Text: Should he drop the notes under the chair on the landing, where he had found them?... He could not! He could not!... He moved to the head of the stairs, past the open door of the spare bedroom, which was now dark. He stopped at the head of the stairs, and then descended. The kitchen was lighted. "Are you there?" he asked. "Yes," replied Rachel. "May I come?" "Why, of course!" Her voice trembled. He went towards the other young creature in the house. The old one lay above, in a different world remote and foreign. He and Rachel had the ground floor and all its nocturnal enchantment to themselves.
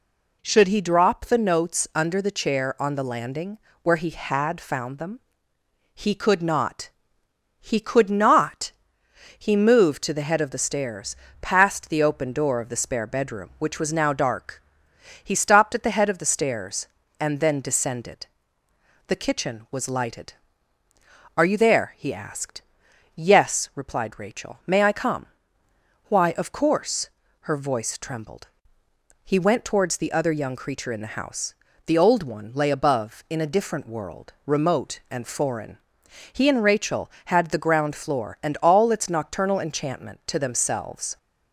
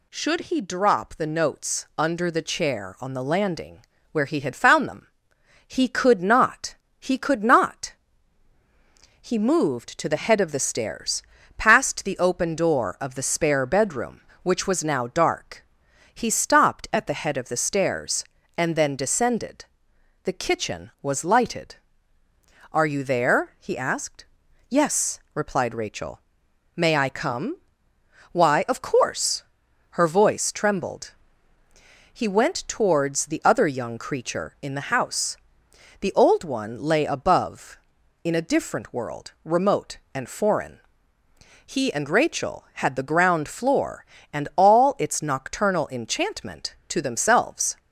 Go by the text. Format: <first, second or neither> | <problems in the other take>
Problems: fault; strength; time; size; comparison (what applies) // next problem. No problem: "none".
neither | none